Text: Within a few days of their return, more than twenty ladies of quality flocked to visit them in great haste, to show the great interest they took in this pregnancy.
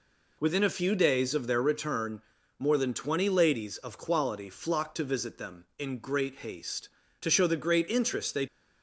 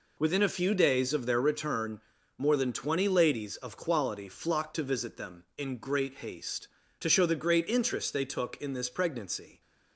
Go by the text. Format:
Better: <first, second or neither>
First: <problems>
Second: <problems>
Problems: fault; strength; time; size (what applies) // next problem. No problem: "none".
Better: second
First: stops before "took in this pregnancy"; at 8.4 s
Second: none